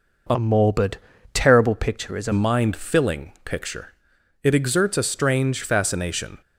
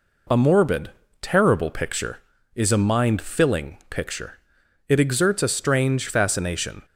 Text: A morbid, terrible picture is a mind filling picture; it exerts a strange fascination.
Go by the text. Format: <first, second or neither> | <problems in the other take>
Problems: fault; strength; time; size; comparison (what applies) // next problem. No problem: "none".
second | changes voice from "morbid" to "a"; from 0.3 to 2.3 s; 2.0 s long